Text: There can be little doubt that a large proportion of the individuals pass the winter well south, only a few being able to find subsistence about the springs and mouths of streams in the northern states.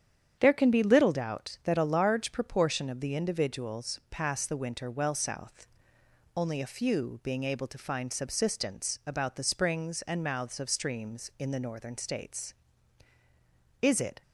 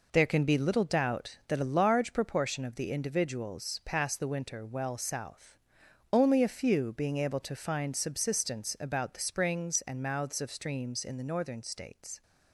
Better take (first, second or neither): second